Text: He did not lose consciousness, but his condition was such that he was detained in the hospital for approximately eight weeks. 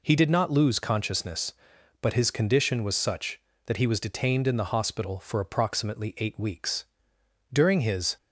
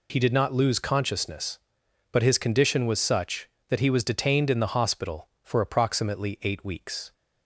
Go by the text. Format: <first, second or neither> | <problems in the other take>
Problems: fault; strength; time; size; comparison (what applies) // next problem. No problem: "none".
second | goes on to say "During his"; noticeable; from 7.5 s on; 0.64 s long